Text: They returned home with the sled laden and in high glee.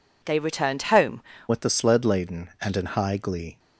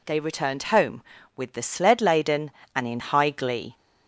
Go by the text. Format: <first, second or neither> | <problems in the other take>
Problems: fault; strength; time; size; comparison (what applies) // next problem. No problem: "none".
second | changes voice at "with"; from 1.4 s on; 2.1 s long